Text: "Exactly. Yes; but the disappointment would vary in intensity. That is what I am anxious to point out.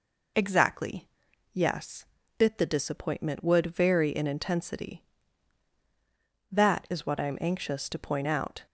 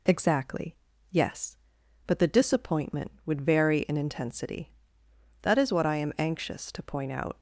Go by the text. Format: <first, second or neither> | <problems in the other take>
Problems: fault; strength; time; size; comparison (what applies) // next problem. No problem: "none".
second | says "bit" for "but"; at 2.3 s